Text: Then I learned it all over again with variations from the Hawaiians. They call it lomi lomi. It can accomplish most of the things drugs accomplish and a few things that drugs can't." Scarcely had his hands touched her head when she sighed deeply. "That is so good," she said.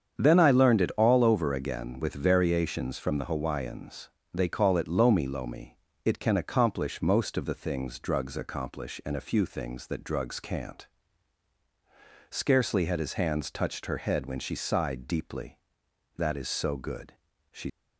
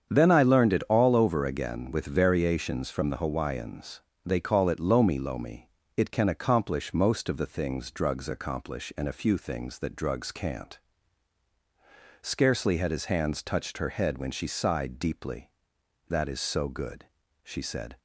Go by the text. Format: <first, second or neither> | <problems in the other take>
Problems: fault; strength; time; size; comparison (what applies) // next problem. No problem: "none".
second | starts louder than the rest; strong; until 1.2 s; 7.5 dB; strong in the second // stops before "said"; at 17.6 s